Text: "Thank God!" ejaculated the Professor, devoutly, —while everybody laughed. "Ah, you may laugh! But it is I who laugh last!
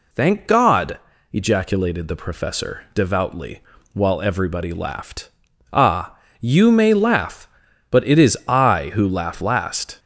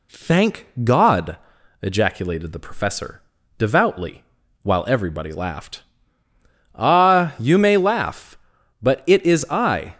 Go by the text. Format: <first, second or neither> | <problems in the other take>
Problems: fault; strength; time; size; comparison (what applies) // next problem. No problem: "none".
first | pauses between "Thank" and "God"; slight; at 0.6 s; 0.16 s long // stops before "who laugh last"; at 9.9 s